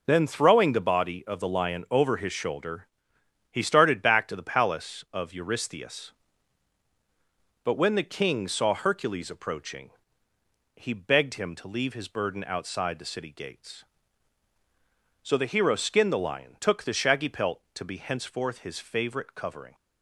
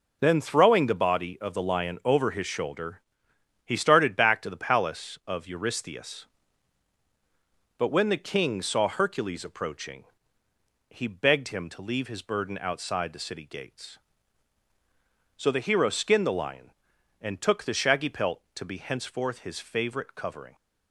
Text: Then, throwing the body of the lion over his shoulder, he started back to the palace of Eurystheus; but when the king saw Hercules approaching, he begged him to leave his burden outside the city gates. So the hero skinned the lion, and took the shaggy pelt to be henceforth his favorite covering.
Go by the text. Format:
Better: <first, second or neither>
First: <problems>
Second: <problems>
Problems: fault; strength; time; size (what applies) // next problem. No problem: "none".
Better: second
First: skips "and"; at 16.5 s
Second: none